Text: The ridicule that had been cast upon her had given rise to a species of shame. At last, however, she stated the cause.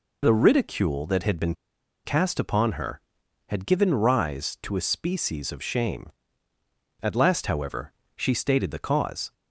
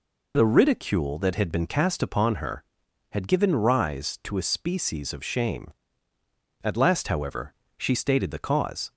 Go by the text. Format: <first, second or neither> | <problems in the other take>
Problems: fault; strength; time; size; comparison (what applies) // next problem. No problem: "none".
second | pauses between "been" and "cast"; noticeable; at 1.5 s; 0.50 s long